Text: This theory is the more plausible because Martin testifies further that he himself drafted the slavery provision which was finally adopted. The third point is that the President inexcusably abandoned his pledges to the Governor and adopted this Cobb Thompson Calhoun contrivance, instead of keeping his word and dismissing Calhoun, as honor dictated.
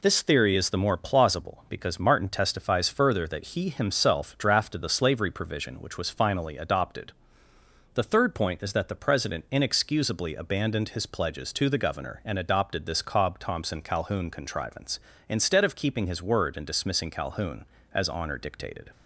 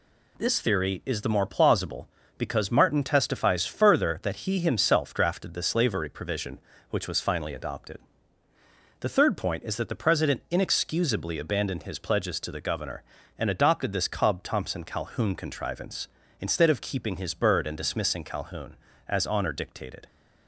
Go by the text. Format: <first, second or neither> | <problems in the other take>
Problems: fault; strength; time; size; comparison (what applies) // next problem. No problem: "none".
first | says "bird" for "word"; at 17.3 s